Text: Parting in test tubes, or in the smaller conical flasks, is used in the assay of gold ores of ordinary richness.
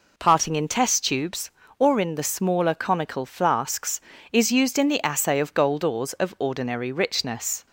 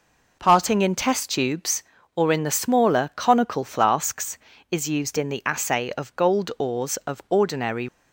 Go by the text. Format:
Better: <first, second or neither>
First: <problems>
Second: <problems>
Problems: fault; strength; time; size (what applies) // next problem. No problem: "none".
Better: first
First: none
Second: stops before "richness"; at 7.8 s